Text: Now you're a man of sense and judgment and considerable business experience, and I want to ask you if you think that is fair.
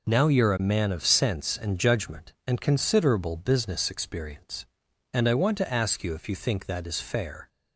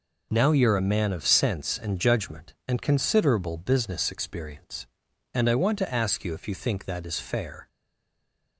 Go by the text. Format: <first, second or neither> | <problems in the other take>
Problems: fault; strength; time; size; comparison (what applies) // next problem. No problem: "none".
first | stays silent after the last word; slight; from 7.6 s on; 0.9 s long